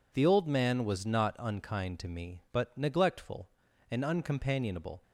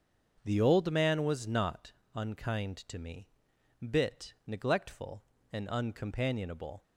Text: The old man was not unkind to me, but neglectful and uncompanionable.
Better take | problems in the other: first | starts louder than the rest; until 1.4 s; 7 dB // pauses between "not" and "unkind"; slight; at 1.9 s; 0.24 s long // says "bit" for "but"; at 3.8 s

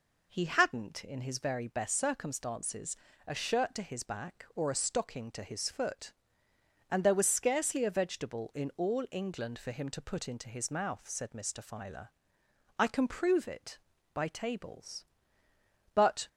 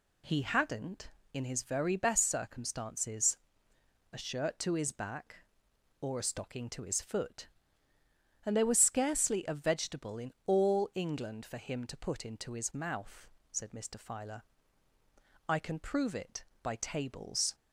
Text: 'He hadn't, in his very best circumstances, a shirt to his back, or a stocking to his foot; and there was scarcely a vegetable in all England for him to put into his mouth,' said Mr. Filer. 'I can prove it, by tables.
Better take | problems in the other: second | goes on to say "But"; slight; from 15.9 s on; 0.34 s long

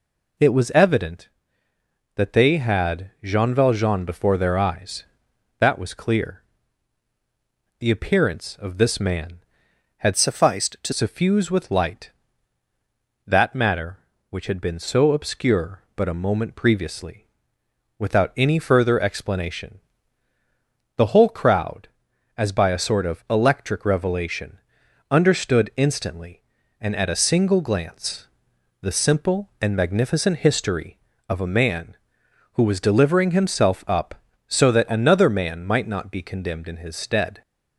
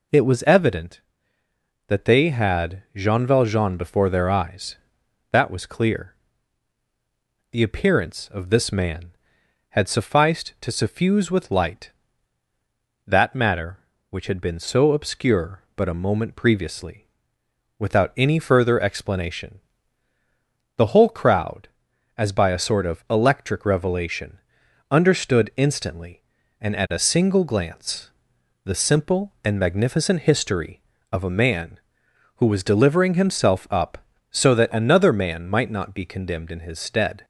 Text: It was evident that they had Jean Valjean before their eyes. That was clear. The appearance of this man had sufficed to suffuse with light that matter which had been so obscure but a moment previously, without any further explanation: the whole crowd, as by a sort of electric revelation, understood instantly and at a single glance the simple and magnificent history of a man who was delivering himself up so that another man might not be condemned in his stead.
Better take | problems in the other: second | changes voice from "sufficed" to "to"; from 10.1 to 10.9 s; 0.8 s long // pauses between "glance" and "the"; noticeable; at 28.2 s; 0.54 s long; noticeable in the second

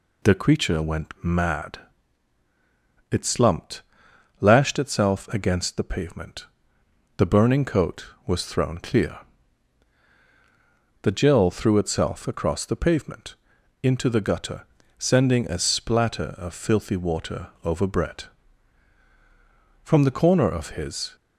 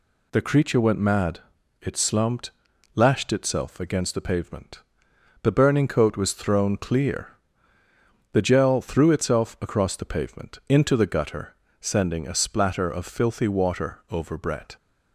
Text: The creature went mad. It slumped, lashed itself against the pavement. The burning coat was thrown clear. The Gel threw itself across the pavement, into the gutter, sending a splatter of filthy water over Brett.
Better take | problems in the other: second | pauses between "water" and "over"; slight; at 17.4 s; 0.16 s long // goes on to say "From the corner of his"; from 19.8 s on; 1.3 s long

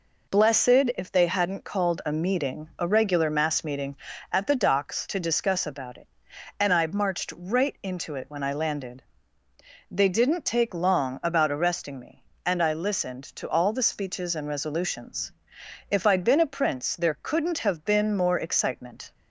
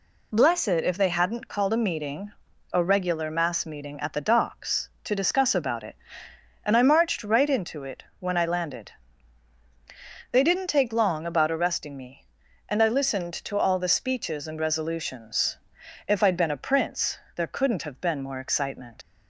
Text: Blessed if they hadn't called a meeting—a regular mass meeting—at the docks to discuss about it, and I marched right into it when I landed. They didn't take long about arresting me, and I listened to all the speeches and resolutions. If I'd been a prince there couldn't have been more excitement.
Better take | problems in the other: first | pauses between "it" and "when"; slight; at 8.0 s; 0.16 s long // pauses between "prince" and "there"; slight; at 17.1 s; 0.18 s long // leaves "excitement" unfinished; at 19.0 s; 110 ms

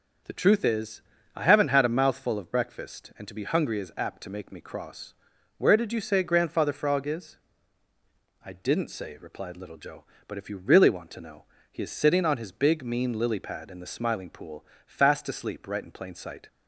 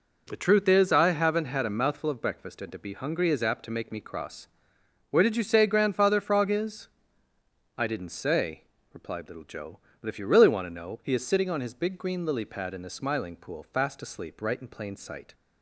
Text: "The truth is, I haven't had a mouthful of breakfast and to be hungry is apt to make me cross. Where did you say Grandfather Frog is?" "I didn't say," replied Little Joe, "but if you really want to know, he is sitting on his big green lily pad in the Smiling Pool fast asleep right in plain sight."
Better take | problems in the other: second | starts louder than the rest; until 1.6 s; 6.5 dB // says "mean" for "green"; at 12.8 s // pauses between "Pool" and "fast"; slight; at 14.6 s; 0.20 s long

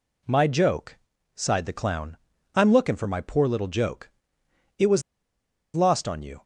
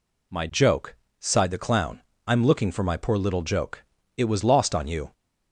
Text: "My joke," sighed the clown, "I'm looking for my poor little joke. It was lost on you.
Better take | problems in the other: second | pauses between "was" and "lost"; noticeable; at 5.0 s; 0.73 s long

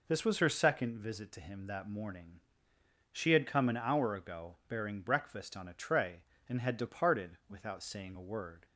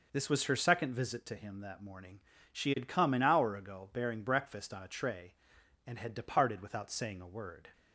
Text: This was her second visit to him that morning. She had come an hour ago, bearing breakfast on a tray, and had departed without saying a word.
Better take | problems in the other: neither | none

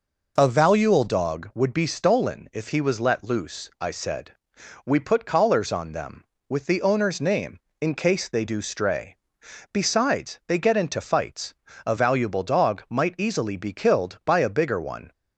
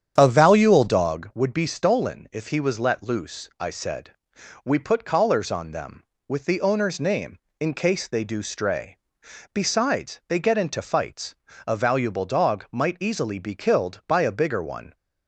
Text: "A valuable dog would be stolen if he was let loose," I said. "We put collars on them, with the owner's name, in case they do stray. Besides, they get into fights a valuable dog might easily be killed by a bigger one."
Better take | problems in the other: first | starts louder than the rest; strong; until 1.3 s; 8.5 dB // pauses between "fights" and "a"; slight; at 11.3 s; 0.32 s long; slight in the first

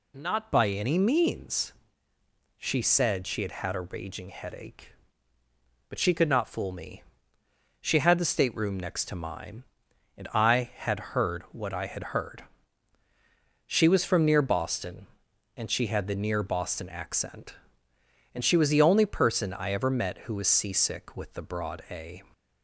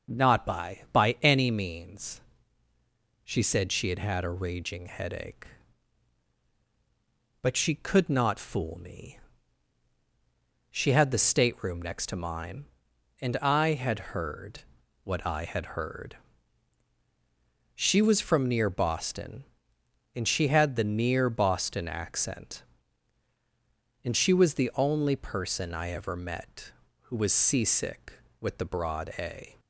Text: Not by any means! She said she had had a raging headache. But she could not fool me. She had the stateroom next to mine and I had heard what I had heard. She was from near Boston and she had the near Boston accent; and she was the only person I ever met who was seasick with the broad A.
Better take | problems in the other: first | starts louder than the rest; until 1.2 s; 6.5 dB // says "by" twice; at 0.9 s // pauses between "heard" and "what"; at 14.6 s; 0.42 s long

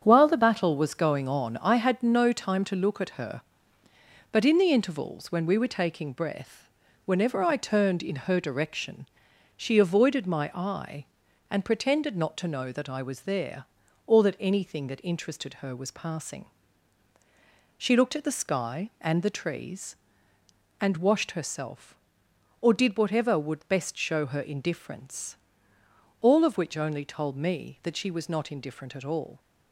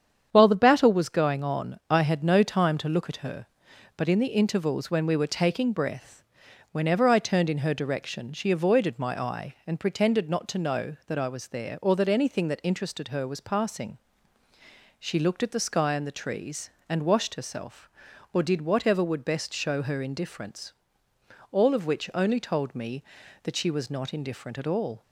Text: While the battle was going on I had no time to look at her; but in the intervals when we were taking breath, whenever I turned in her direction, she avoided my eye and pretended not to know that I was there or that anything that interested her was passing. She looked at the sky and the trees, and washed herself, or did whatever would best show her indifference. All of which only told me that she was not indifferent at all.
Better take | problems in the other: neither | starts louder than the rest; strong; the same in both

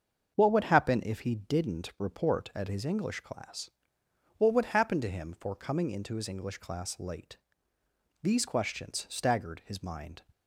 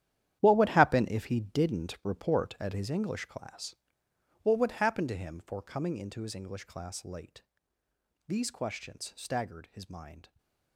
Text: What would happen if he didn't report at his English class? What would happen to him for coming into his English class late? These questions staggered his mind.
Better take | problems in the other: first | gets quieter; strong; throughout; 12.5 dB // starts louder than the rest; strong; until 1.4 s; 11 dB; also in the first // stays silent after the last word; slight; from 10.2 s on; 0.5 s long

